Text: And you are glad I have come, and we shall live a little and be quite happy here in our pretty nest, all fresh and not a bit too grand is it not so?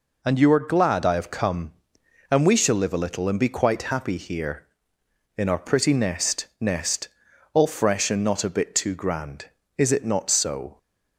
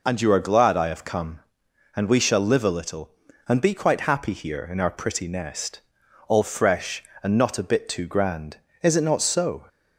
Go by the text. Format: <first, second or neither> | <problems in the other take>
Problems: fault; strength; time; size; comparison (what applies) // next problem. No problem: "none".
second | says "nest" twice; at 6.5 s